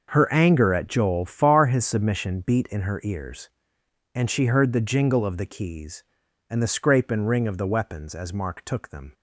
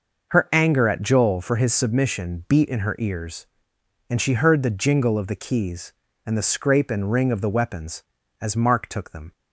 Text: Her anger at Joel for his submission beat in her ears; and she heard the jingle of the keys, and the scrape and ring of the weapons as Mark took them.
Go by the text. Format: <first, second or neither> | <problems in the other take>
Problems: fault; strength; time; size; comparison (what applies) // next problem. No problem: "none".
second | says "far" for "for"; at 1.2 s